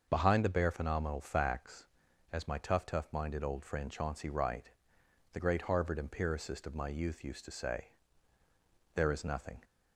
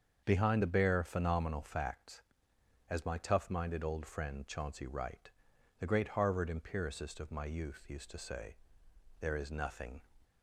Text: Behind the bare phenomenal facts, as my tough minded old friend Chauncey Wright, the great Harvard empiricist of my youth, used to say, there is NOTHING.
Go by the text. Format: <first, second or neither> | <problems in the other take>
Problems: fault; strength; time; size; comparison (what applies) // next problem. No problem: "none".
second | starts louder than the rest; until 1.1 s; 6 dB; also in the second // says "tough" twice; at 2.8 s